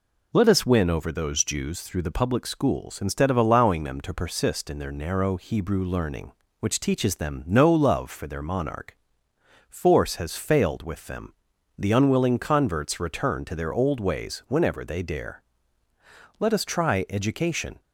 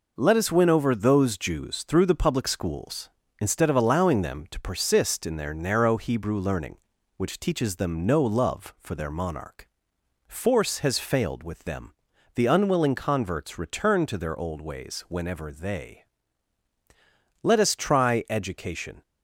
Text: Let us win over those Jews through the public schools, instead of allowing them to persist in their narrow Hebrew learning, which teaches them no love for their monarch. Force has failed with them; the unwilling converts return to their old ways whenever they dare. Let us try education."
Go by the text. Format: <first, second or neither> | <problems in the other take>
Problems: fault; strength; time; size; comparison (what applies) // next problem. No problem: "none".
first | skips "dare"; at 16.7 s